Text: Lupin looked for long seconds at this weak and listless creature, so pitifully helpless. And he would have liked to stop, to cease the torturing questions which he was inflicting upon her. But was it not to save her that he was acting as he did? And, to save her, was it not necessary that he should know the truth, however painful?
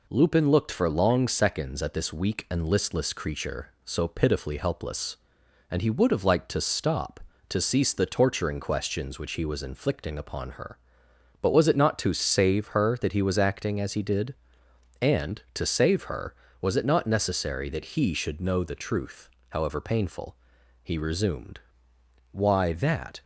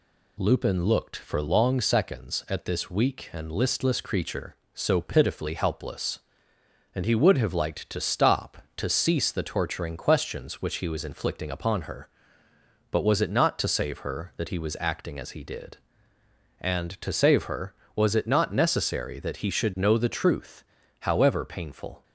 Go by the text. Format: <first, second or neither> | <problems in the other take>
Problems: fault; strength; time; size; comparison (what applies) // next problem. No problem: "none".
second | goes on to say "He resumed Why that"; strong; from 20.8 s on; 2.3 s long